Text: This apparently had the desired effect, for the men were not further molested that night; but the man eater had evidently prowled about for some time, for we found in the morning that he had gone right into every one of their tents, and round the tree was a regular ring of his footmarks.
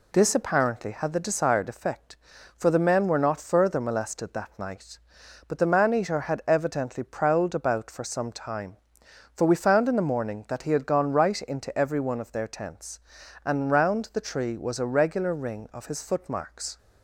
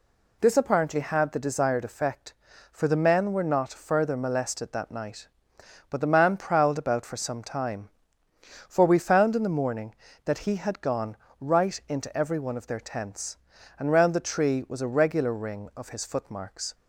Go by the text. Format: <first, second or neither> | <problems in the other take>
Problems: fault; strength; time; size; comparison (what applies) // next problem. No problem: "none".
first | skips "eater had evidently"; at 6.3 s // pauses between "gone" and "right"; slight; at 11.1 s; 0.24 s long